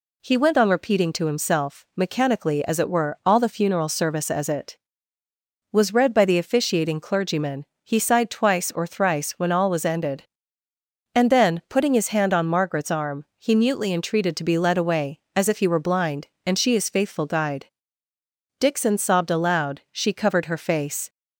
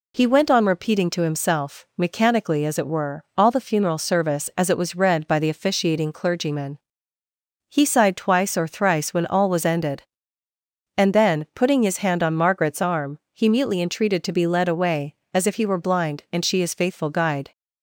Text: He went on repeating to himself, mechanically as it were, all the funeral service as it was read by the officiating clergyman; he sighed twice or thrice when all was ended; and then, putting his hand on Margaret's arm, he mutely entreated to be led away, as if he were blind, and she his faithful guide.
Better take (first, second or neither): second